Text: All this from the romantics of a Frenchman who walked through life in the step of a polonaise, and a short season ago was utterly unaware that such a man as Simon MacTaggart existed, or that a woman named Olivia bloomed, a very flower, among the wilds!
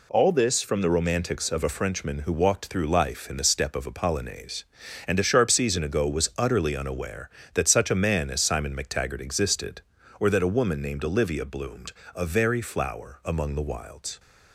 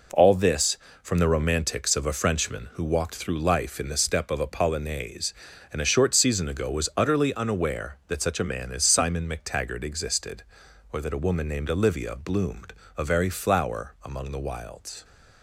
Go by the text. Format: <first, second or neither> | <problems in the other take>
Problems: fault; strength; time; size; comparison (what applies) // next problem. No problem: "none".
second | says "sharp" for "short"; at 5.2 s